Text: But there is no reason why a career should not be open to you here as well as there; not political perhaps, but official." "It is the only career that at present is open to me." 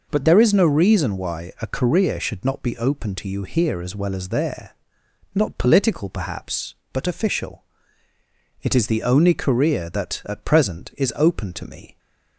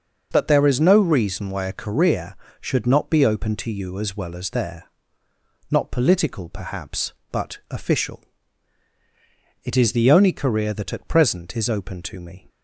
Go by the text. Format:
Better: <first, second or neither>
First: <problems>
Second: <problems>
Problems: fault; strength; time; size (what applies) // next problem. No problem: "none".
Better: first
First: none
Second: starts louder than the rest; until 1.3 s; 6 dB // skips "here"; at 3.9 s